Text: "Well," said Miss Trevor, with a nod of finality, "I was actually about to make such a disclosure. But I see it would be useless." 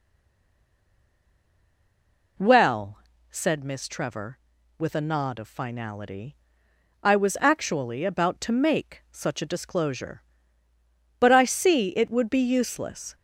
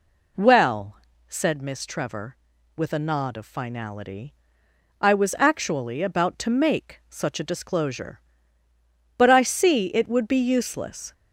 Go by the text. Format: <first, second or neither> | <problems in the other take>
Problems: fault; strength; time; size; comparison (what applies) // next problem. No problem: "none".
second | stays silent before the first word; until 2.3 s; 2.3 s long